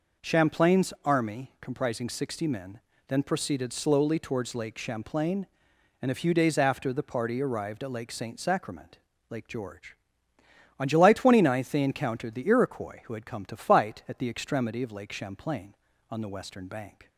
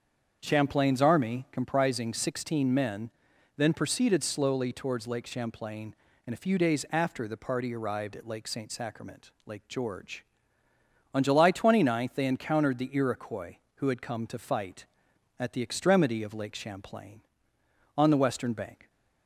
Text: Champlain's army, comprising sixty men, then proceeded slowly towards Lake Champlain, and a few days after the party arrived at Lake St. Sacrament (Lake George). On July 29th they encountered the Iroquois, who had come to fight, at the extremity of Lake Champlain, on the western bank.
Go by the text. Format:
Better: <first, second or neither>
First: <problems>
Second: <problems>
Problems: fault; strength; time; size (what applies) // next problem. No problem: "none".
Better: first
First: none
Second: starts louder than the rest; strong; until 1.4 s; 7.5 dB // says "sixteen" for "sixty"; at 2.1 s